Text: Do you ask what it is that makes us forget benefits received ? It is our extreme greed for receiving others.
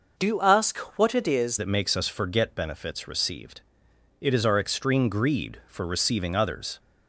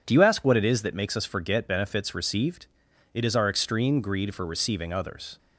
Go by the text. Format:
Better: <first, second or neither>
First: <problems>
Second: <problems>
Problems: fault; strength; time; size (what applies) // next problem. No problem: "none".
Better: second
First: changes voice from "you" to "is"; from 0.2 to 1.5 s; 1.3 s long // pauses between "ask" and "what"; slight; at 0.7 s; 0.18 s long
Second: none